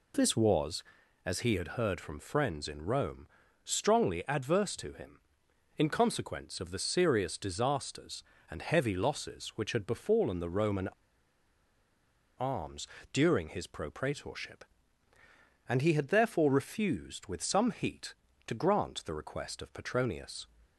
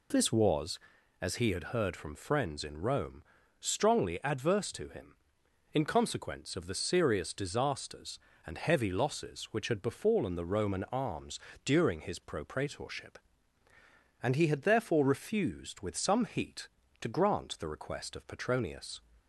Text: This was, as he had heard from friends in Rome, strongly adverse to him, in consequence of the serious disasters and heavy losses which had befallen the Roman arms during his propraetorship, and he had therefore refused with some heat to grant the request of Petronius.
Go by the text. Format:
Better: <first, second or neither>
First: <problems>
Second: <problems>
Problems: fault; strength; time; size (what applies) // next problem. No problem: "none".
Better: second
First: pauses between "Roman" and "arms"; strong; at 10.8 s; 1.5 s long // pauses between "arms" and "during"; slight; at 12.8 s; 0.24 s long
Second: pauses between "arms" and "during"; slight; at 11.3 s; 0.24 s long